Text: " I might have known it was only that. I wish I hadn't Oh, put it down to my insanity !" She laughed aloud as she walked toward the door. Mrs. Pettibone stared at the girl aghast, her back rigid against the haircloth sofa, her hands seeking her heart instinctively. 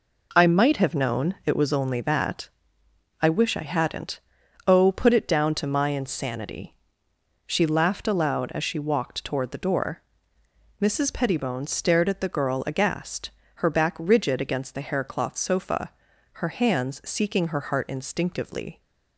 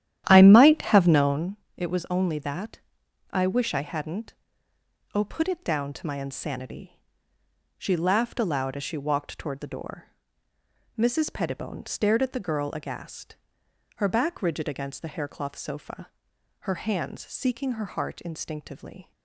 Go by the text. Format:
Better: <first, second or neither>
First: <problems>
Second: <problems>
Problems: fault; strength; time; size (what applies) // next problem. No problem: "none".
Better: first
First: pauses between "hadn't" and "Oh"; at 4.2 s; 0.44 s long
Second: starts louder than the rest; strong; until 1.6 s; 11.5 dB // pauses between "known" and "it"; slight; at 1.5 s; 0.22 s long // pauses between "hadn't" and "Oh"; noticeable; at 4.3 s; 0.80 s long